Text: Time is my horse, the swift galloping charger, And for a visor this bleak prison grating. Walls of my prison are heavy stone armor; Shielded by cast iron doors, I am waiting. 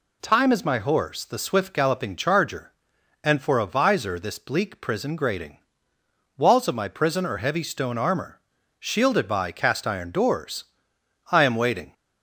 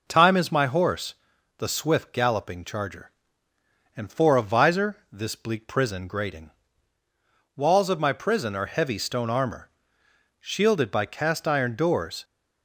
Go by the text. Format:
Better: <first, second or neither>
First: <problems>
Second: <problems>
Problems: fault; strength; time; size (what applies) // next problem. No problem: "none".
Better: first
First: none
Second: pauses between "visor" and "this"; slight; at 4.9 s; 0.16 s long // stops before "I am waiting"; at 12.2 s